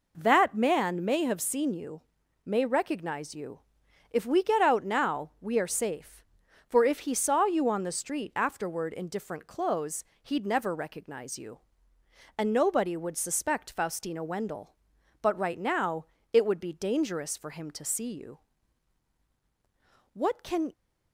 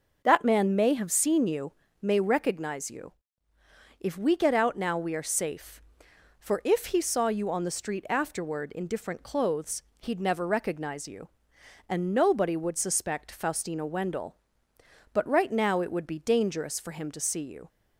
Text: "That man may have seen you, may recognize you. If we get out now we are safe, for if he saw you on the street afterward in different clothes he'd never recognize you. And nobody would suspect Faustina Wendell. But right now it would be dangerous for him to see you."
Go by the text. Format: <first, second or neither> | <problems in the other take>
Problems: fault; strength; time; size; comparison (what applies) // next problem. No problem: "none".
second | pauses between "clothes" and "he'd"; slight; at 10.0 s; 0.18 s long; slight in the second // pauses between "now" and "it"; slight; at 16.0 s; 0.26 s long // goes on to say "What can"; from 20.1 s on; 0.58 s long